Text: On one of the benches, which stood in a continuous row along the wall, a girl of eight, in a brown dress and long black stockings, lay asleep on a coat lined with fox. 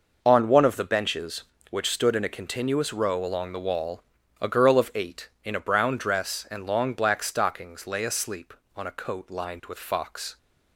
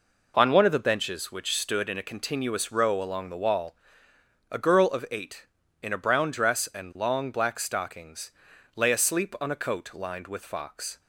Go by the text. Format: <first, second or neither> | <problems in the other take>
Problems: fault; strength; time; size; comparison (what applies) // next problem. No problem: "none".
neither | none